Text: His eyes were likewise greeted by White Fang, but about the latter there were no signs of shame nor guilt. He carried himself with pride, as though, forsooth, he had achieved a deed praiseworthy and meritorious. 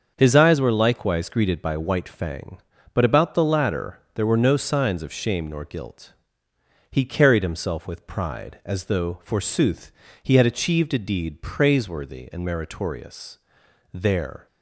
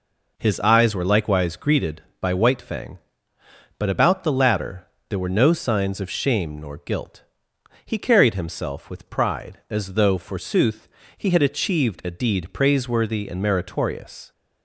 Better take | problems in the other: second | starts louder than the rest; until 1.1 s; 6.5 dB // pauses between "latter" and "there"; slight; at 3.9 s; 0.16 s long; slight in the second // goes on to say "There"; from 13.9 s on; 0.54 s long

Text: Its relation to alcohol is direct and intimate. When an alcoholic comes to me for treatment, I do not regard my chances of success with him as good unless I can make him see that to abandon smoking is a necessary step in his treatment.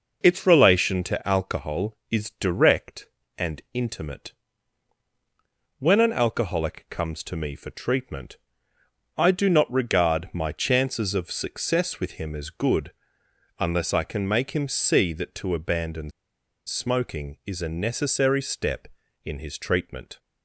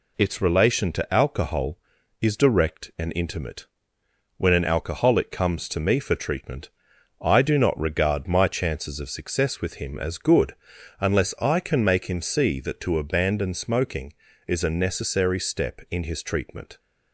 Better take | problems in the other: second | pauses between "good" and "unless"; noticeable; at 12.9 s; 0.68 s long; noticeable in the second // pauses between "abandon" and "smoking"; noticeable; at 16.1 s; 0.55 s long

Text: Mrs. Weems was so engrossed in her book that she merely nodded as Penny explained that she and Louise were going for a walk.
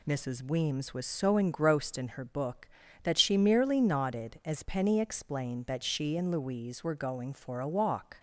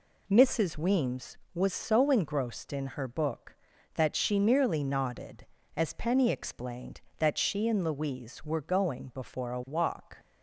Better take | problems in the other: first | says "before" for "for"; at 9.1 s

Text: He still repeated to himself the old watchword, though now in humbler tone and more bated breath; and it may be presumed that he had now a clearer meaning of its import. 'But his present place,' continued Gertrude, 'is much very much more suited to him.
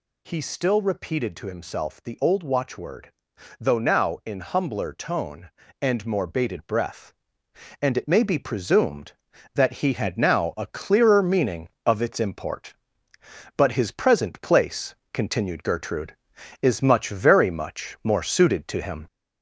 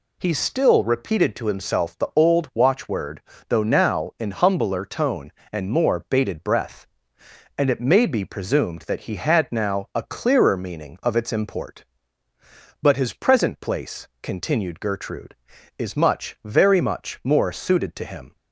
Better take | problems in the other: second | gets louder; slight; throughout; 3 dB

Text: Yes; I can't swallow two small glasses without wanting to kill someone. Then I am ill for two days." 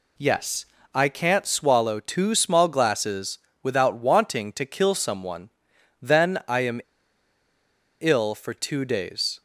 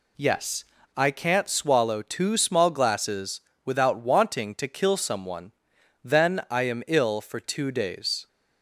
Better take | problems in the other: second | pauses between "glasses" and "without"; slight; at 3.3 s; 0.24 s long; slight in the second // pauses between "am" and "ill"; at 6.8 s; 1.2 s long

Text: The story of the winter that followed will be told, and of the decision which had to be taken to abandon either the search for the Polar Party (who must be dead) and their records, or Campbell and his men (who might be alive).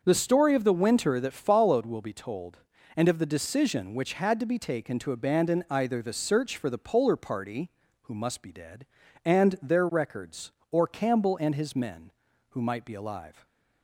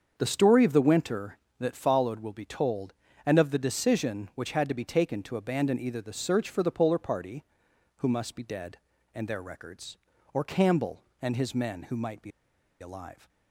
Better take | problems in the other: first | starts louder than the rest; until 1.1 s; 7 dB; also in the first // pauses between "be" and "alive"; noticeable; at 12.3 s; 0.50 s long

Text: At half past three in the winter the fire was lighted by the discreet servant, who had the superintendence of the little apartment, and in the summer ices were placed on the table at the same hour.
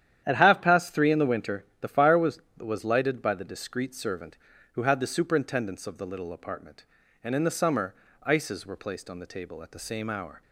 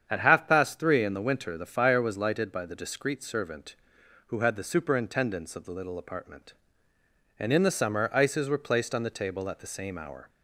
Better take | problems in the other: second | starts louder than the rest; strong; until 1.2 s; 10 dB; strong in the second // pauses between "winter" and "the"; slight; at 1.6 s; 0.16 s long // says "was" twice; at 2.5 s // pauses between "summer" and "ices"; slight; at 7.9 s; 0.30 s long

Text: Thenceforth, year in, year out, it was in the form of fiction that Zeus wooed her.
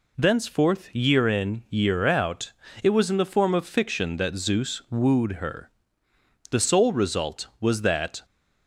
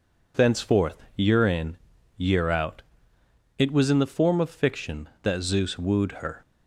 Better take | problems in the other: second | goes on to say "The sole result was that"; strong; from 6.5 s on; 1.7 s long

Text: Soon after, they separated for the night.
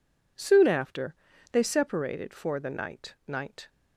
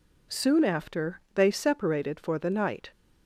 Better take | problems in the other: second | says "night" twice; at 3.2 s

